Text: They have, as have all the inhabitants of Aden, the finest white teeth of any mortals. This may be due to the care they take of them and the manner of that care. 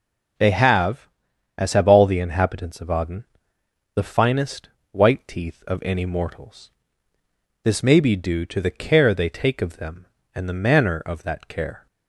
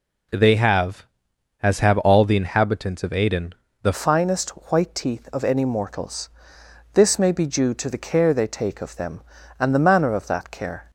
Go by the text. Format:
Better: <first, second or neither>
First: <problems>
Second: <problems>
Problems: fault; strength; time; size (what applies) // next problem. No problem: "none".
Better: first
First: pauses between "finest" and "white"; slight; at 4.6 s; 0.24 s long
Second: changes voice at "finest"; from 3.9 s on; 7.0 s long // pauses between "finest" and "white"; slight; at 4.5 s; 0.20 s long